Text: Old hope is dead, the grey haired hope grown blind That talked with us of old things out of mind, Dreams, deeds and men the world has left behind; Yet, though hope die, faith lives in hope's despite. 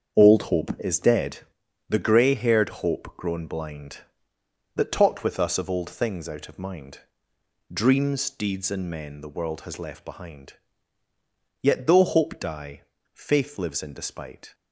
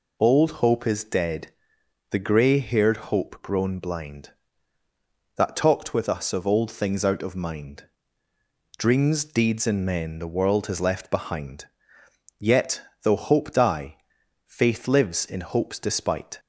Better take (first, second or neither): second